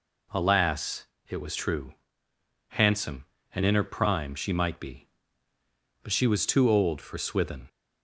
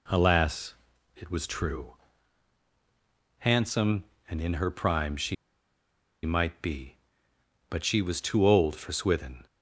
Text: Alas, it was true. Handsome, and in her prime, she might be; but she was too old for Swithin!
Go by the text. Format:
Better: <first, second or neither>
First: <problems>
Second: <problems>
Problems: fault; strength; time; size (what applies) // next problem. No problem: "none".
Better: first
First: none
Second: pauses between "she" and "might"; noticeable; at 5.3 s; 0.89 s long